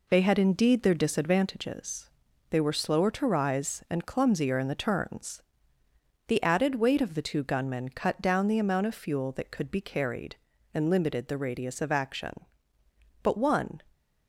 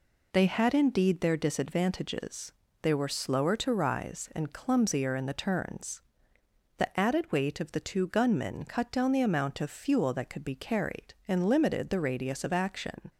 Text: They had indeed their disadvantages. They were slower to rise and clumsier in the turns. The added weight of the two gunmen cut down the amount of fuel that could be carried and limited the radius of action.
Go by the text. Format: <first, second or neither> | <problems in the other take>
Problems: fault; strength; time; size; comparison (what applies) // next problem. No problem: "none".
second | goes on to say "But one"; from 13.2 s on; 0.58 s long